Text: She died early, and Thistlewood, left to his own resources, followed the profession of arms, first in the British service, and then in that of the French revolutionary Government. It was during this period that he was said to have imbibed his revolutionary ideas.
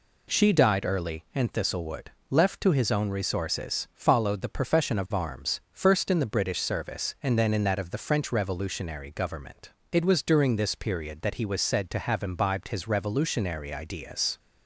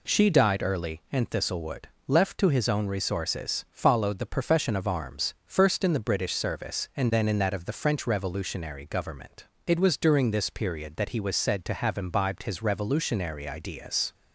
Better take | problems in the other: neither | none

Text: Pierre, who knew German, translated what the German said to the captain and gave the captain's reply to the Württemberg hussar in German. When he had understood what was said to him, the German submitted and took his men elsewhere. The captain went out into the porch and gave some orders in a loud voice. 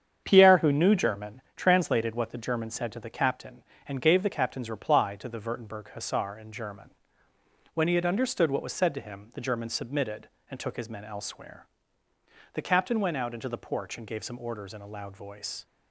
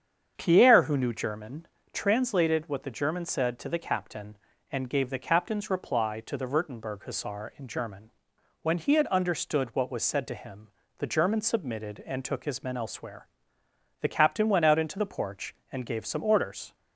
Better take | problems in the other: first | starts louder than the rest; strong; until 1.3 s; 7.5 dB; strong in the first // stops before "in a loud voice"; at 16.7 s

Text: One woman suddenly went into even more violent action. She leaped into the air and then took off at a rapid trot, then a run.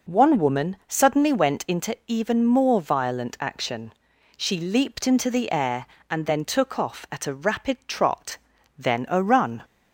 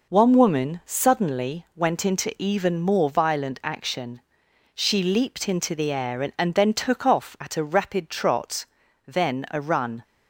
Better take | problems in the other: first | says "and" twice; at 6.3 s

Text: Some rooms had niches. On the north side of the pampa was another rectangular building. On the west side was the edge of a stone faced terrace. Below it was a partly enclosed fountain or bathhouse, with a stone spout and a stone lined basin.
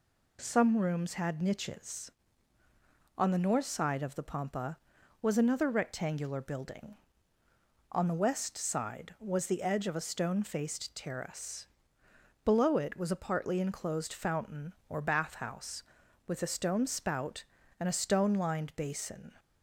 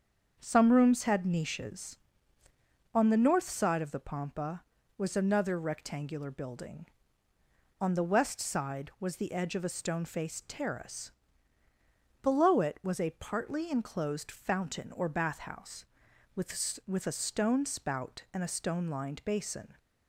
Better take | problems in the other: first | starts louder than the rest; until 1.4 s; 7 dB // says "with" twice; at 16.8 s

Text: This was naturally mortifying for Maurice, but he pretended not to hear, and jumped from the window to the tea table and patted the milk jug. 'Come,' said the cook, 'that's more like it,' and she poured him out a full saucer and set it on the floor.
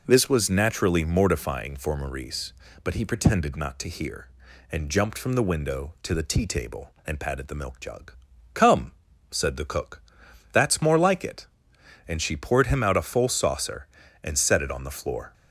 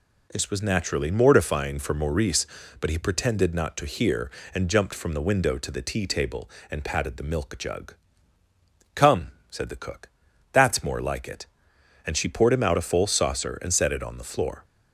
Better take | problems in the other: neither | none

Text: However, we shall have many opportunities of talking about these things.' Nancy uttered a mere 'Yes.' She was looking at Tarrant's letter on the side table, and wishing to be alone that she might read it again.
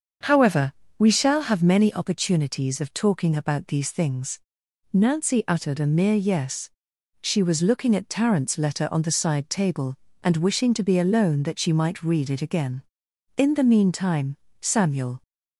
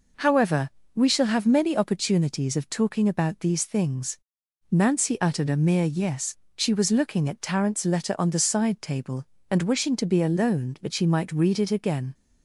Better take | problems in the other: second | starts louder than the rest; until 1.4 s; 6.5 dB // goes on to say "In the meantime Samuel"; strong; from 13.3 s on; 1.8 s long

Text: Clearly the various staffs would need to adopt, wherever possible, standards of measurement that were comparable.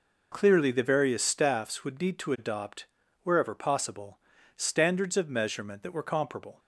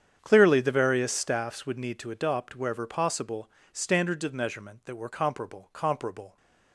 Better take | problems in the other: first | starts louder than the rest; strong; until 1.2 s; 8.5 dB // says "comparable" twice; at 5.7 s

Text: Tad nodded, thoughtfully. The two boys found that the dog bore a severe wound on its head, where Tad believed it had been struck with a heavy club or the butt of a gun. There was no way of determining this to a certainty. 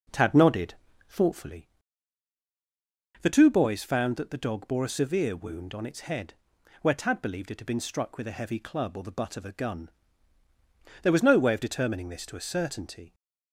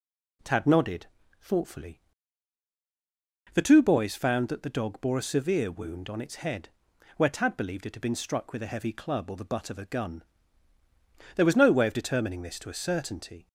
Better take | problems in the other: second | starts louder than the rest; noticeable; until 1.5 s; 5 dB

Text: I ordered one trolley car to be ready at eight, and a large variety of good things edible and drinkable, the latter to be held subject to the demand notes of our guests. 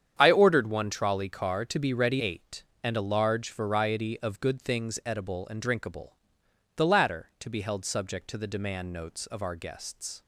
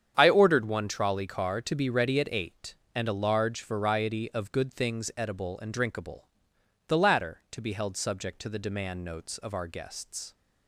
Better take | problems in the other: second | starts louder than the rest; strong; until 1.2 s; 8.5 dB; strong in the second // skips "at"; at 2.2 s

